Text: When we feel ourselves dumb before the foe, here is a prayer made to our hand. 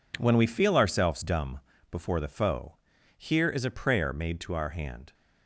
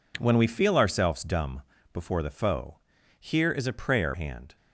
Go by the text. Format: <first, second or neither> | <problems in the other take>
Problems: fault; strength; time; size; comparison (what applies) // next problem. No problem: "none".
first | pauses between "dumb" and "before"; slight; at 1.6 s; 0.30 s long; slight in the first // skips "made to our"; at 4.1 s